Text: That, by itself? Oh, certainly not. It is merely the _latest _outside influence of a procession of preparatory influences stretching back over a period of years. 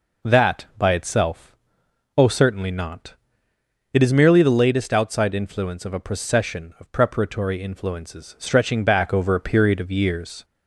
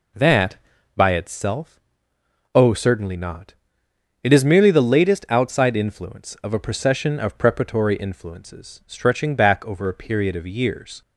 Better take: neither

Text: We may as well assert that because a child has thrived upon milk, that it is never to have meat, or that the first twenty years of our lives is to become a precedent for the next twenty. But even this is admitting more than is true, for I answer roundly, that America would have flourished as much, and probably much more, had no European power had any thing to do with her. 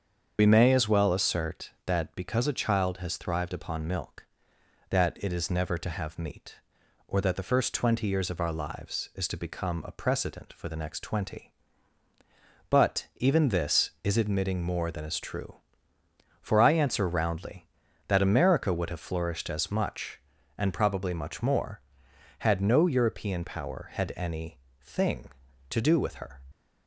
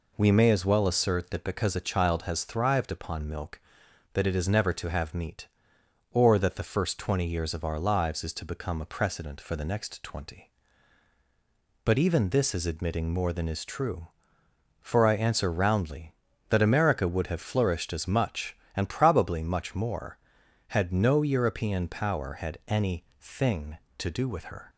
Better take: second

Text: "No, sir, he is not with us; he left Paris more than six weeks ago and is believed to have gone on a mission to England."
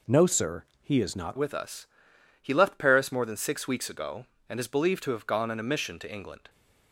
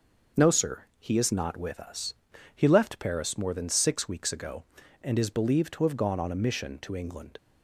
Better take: second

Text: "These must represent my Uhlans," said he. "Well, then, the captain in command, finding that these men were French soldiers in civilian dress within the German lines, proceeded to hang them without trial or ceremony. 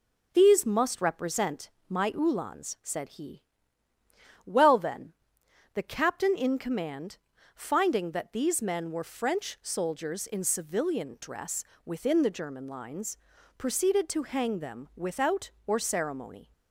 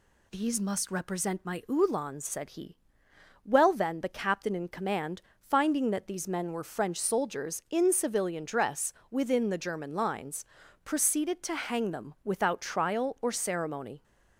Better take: second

